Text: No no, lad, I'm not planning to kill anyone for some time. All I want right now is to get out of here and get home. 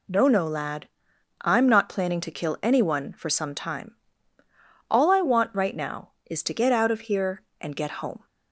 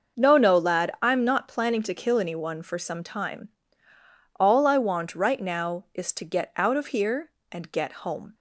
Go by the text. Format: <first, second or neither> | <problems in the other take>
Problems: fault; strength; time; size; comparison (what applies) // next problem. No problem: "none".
neither | none